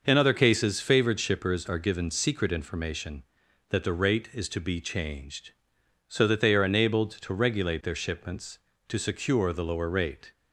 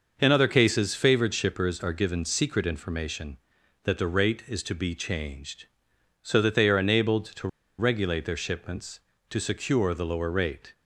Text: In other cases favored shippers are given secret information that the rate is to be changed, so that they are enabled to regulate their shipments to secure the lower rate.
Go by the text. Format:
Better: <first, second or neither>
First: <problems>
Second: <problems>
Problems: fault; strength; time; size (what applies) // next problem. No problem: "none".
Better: first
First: none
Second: pauses between "to" and "regulate"; slight; at 7.4 s; 0.29 s long